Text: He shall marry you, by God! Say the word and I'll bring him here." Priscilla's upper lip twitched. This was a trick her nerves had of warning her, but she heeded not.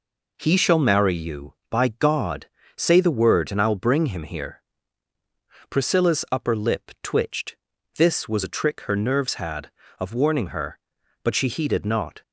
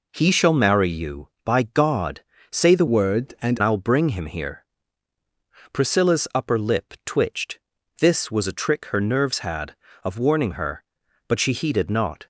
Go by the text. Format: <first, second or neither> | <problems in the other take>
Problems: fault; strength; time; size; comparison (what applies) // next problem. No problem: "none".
first | changes voice from "word" to "and"; from 2.8 to 3.5 s; 0.7 s long